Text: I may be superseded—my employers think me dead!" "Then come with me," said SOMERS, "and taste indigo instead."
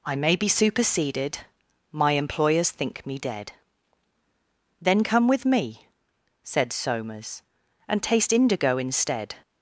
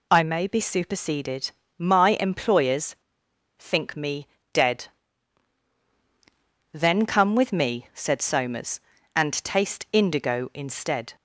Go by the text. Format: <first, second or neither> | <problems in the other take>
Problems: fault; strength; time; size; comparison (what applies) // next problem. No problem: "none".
first | pauses between "employers" and "think"; noticeable; at 2.9 s; 0.64 s long // pauses between "me" and "dead"; slight; at 4.2 s; 0.24 s long